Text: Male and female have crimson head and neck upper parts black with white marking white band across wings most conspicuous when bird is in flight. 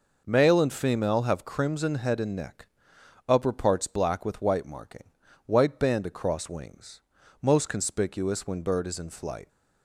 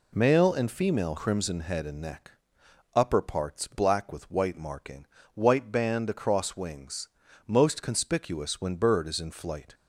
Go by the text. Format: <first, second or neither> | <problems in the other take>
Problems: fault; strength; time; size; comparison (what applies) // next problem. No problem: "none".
first | skips "have"; at 1.1 s // pauses between "neck" and "upper"; noticeable; at 2.3 s; 0.64 s long; noticeable in the first // pauses between "marking" and "white"; slight; at 5.0 s; 0.28 s long; also in the first // pauses between "wings" and "most"; slight; at 7.0 s; 0.36 s long; also in the first